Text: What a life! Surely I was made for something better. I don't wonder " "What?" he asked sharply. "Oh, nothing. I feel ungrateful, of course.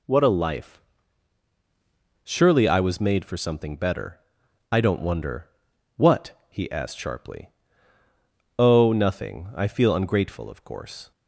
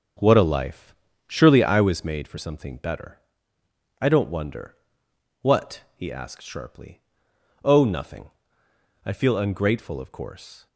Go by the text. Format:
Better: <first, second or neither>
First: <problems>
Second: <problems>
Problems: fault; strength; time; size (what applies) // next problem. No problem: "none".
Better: first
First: none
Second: starts louder than the rest; until 2.0 s; 7 dB